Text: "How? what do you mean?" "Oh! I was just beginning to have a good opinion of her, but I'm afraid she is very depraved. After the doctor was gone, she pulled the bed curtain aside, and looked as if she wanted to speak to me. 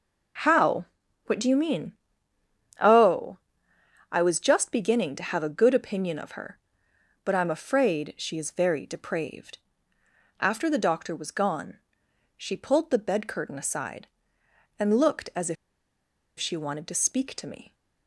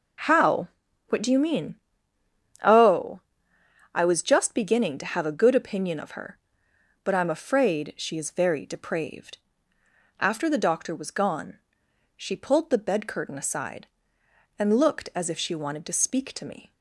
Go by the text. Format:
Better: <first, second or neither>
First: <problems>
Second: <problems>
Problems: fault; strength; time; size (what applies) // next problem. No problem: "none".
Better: second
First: pauses between "if" and "she"; noticeable; at 15.5 s; 0.84 s long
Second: none